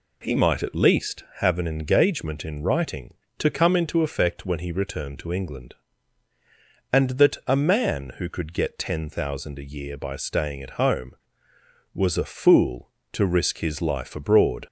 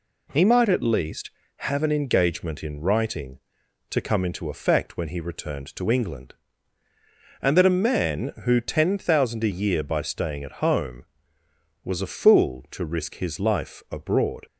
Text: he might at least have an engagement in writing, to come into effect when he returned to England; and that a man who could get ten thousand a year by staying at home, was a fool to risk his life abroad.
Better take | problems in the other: first | skips "could get"; at 8.5 s

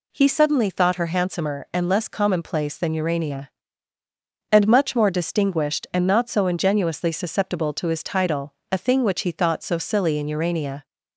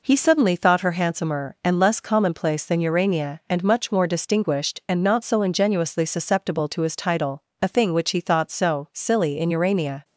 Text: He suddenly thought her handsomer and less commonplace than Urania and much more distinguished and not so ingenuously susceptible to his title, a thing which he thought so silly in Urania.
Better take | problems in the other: neither | none

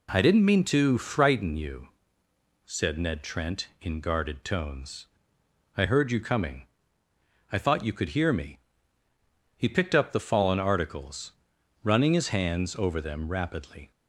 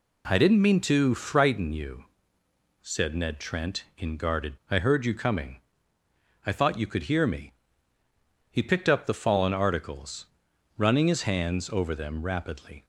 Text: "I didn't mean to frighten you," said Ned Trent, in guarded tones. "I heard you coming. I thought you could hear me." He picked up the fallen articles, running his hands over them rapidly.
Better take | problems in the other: first | skips "tones"; at 4.6 s

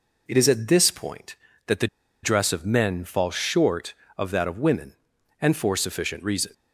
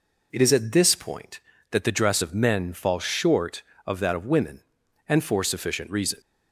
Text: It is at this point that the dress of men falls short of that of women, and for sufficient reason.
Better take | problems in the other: second | pauses between "the" and "dress"; slight; at 1.8 s; 0.36 s long

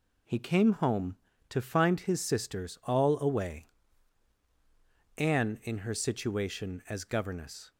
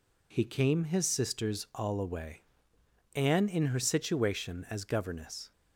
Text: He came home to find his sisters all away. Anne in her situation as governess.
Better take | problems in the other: first | skips "home to find"; at 0.8 s

